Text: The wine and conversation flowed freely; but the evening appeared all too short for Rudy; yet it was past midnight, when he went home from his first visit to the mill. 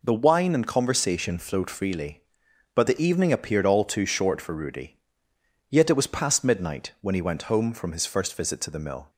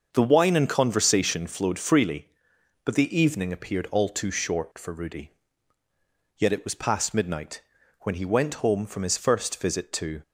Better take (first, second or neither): first